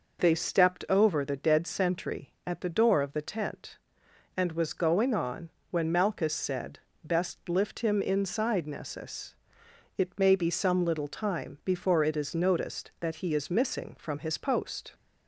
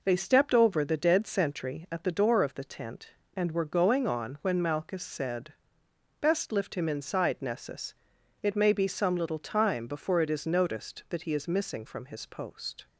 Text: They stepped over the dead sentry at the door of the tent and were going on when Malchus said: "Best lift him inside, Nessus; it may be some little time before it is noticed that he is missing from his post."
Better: second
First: says "was" for "were"; at 4.5 s // pauses between "on" and "when"; slight; at 5.4 s; 0.22 s long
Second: none

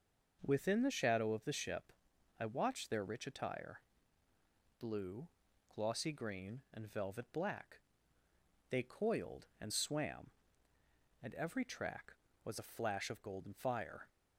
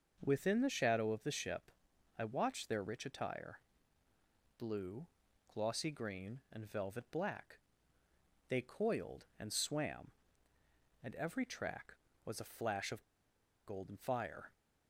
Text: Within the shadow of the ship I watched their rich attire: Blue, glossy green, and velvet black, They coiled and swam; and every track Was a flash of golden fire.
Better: first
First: starts louder than the rest; until 1.4 s; 6 dB // pauses between "ship" and "I"; noticeable; at 1.9 s; 0.48 s long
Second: starts louder than the rest; until 1.2 s; 6 dB // pauses between "ship" and "I"; noticeable; at 1.7 s; 0.48 s long // pauses between "of" and "golden"; noticeable; at 13.0 s; 0.61 s long

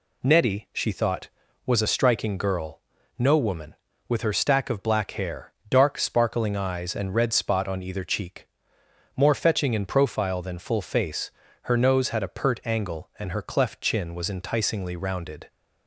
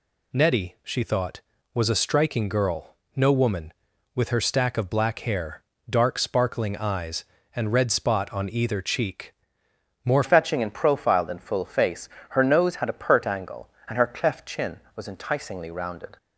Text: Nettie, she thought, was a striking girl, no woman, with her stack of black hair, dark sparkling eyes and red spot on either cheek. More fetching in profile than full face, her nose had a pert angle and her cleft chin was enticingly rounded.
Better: first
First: none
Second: changes voice at "fetching"; from 10.2 s on; 5.9 s long

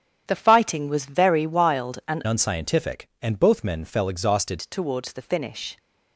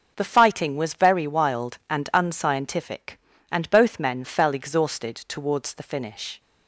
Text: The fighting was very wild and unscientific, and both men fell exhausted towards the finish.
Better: second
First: starts louder than the rest; strong; until 1.2 s; 9.5 dB // changes voice from "unscientific" to "exhausted"; from 2.2 to 4.5 s; 2.3 s long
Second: none

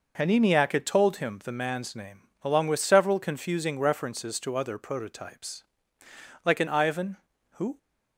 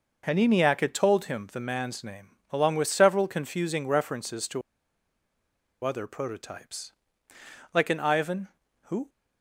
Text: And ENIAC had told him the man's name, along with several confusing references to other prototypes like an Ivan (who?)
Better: first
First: pauses between "prototypes" and "like"; noticeable; at 5.6 s; 0.82 s long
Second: pauses between "to" and "other"; at 4.6 s; 1.2 s long // pauses between "prototypes" and "like"; noticeable; at 6.9 s; 0.82 s long

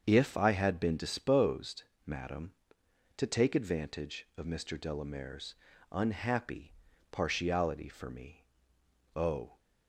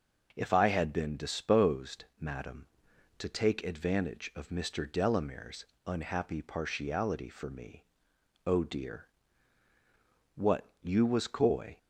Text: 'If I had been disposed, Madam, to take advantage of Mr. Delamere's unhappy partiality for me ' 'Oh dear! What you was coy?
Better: second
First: starts louder than the rest; strong; until 1.0 s; 7 dB // pauses between "Delamere's" and "unhappy"; at 5.5 s; 0.38 s long // pauses between "unhappy" and "partiality"; at 6.7 s; 0.38 s long // stops before "dear What you was coy"; at 9.5 s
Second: starts louder than the rest; until 1.3 s; 6.5 dB // pauses between "Delamere's" and "unhappy"; slight; at 5.6 s; 0.22 s long

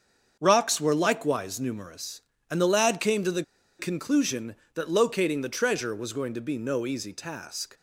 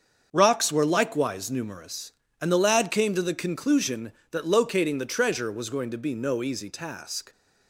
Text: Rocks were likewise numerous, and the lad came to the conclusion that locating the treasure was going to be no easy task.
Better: second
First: starts louder than the rest; until 1.4 s; 7 dB // pauses between "the" and "conclusion"; at 3.4 s; 0.37 s long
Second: starts louder than the rest; until 1.3 s; 7 dB

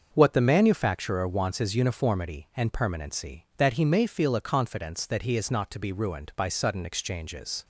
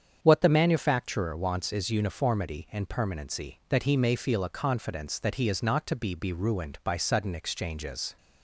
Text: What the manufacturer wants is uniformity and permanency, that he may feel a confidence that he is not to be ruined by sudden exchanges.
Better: first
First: starts louder than the rest; until 1.1 s; 6.5 dB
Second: starts louder than the rest; strong; until 1.2 s; 7.5 dB // says "be" twice; at 6.1 s

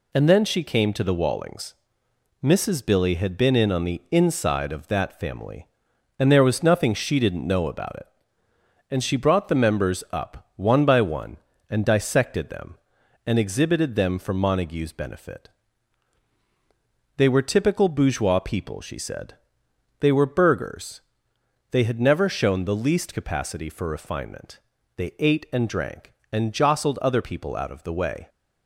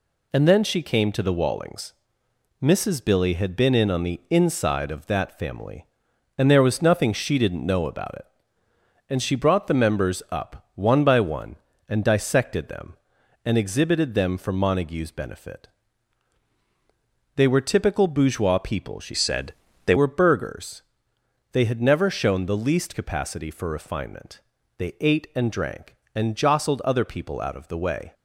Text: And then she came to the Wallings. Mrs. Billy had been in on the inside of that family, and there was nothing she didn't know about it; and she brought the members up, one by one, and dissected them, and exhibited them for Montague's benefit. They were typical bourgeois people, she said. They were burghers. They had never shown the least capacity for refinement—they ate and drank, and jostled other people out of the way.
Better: first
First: none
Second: changes voice from "said" to "They"; from 19.1 to 19.9 s; 0.8 s long

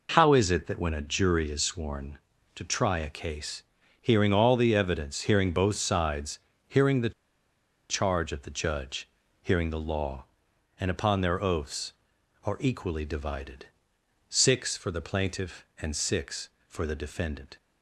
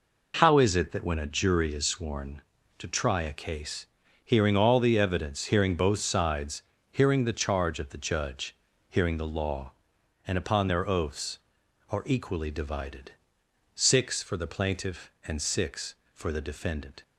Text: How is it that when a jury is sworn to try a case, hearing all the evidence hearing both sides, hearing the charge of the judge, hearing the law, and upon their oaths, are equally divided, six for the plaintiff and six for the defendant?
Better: second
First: pauses between "the" and "charge"; noticeable; at 7.1 s; 0.79 s long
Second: none

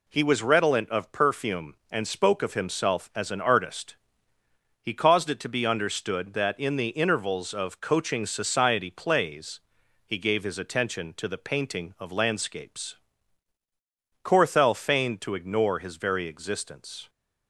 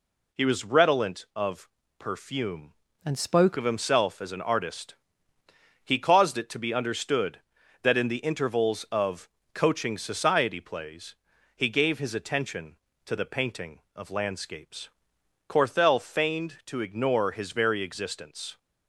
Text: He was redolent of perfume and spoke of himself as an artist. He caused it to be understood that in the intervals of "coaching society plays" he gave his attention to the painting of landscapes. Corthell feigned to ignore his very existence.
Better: first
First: pauses between "plays" and "he"; noticeable; at 9.5 s; 0.46 s long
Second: pauses between "of" and "perfume"; slight; at 1.6 s; 0.30 s long // changes voice from "and" to "spoke"; from 3.0 to 3.5 s; 0.5 s long // pauses between "of" and "coaching"; slight; at 9.2 s; 0.24 s long // pauses between "plays" and "he"; at 11.1 s; 0.40 s long

